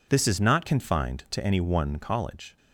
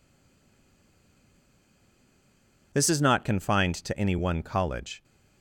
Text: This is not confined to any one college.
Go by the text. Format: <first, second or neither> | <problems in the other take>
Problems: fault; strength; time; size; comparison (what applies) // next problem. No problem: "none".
first | stays silent before the first word; strong; until 2.7 s; 2.7 s long